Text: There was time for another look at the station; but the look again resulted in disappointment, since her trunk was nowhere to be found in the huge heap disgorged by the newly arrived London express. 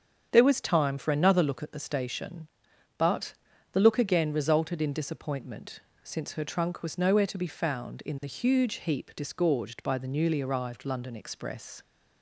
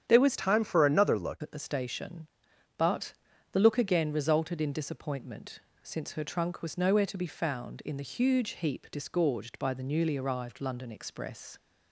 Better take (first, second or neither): first